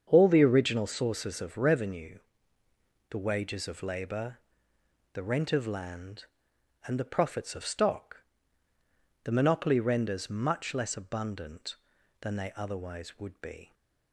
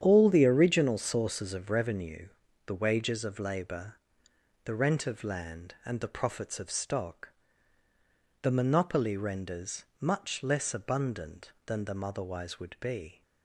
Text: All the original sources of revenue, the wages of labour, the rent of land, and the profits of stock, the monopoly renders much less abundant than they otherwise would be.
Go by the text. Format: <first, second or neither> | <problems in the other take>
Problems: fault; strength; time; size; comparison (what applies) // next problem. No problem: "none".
first | starts louder than the rest; strong; until 1.0 s; 9 dB; strong in the first // pauses between "renders" and "much"; slight; at 9.8 s; 0.16 s long // says "them" for "they"; at 11.8 s